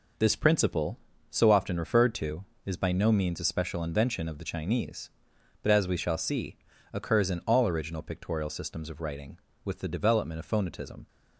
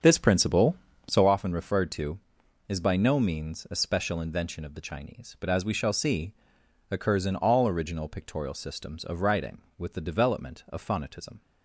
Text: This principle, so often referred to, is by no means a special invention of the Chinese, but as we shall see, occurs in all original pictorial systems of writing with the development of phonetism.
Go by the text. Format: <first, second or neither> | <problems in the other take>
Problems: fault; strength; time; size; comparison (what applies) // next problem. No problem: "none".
first | starts louder than the rest; strong; until 1.3 s; 7 dB